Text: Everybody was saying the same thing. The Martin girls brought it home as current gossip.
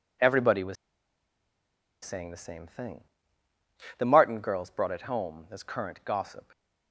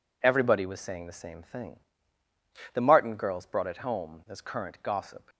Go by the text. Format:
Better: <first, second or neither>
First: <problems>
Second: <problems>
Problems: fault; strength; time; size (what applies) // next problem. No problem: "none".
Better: second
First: pauses between "was" and "saying"; strong; at 0.7 s; 1.2 s long // stays silent after the last word; slight; from 6.4 s on; 0.5 s long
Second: none